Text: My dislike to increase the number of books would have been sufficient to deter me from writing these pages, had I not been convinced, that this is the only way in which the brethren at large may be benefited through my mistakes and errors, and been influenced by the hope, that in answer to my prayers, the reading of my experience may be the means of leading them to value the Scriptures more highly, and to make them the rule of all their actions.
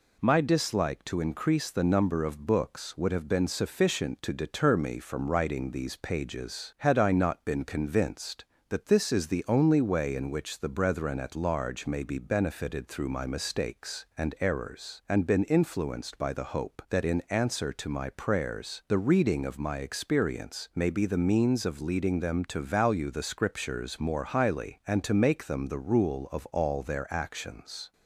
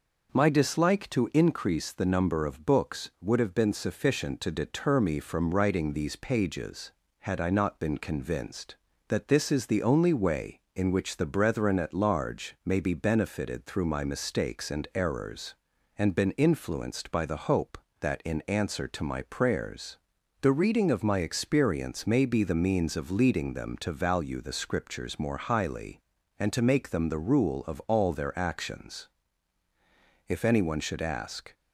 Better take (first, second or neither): first